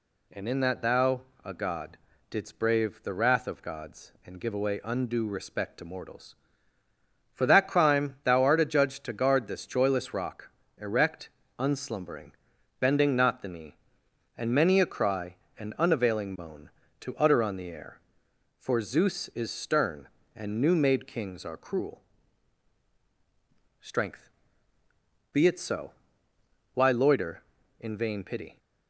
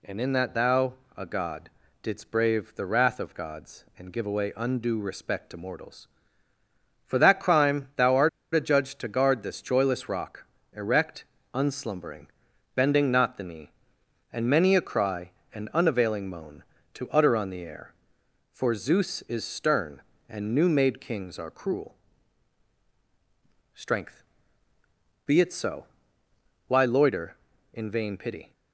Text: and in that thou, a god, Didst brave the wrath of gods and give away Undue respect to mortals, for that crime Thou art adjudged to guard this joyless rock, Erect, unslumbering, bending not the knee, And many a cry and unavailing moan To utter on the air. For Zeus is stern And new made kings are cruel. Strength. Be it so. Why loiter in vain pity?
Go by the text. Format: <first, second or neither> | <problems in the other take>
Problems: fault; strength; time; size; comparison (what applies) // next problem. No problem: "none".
first | pauses between "art" and "adjudged"; slight; at 8.2 s; 0.24 s long